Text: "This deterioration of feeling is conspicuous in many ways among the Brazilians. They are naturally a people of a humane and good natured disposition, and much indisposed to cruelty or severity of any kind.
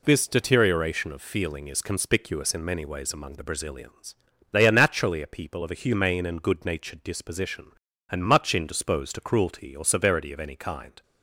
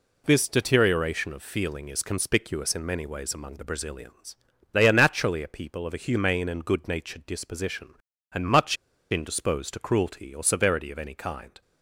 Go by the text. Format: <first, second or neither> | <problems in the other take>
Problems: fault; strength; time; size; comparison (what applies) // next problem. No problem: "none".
first | pauses between "much" and "indisposed"; at 8.7 s; 0.36 s long